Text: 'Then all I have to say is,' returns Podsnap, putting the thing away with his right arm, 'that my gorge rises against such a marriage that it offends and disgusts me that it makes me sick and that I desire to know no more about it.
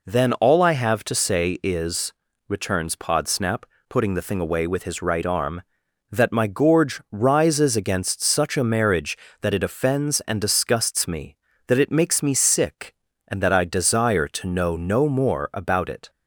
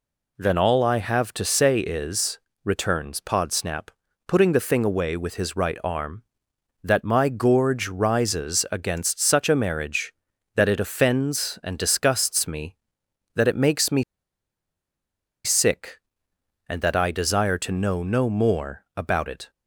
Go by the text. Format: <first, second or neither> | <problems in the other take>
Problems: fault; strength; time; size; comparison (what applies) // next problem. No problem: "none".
first | pauses between "me" and "sick"; strong; at 14.0 s; 1.4 s long